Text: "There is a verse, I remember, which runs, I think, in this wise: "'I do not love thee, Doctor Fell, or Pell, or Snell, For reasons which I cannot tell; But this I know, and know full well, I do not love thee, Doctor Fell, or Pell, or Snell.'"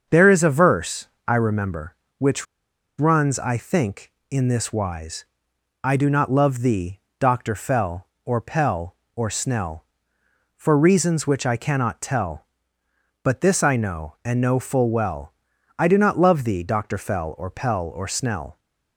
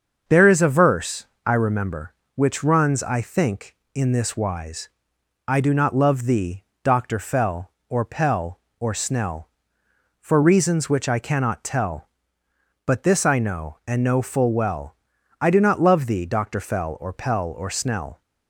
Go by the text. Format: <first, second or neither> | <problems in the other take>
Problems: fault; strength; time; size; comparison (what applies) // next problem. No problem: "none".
second | starts louder than the rest; until 1.2 s; 6.5 dB; also in the second // pauses between "which" and "runs"; noticeable; at 2.4 s; 0.53 s long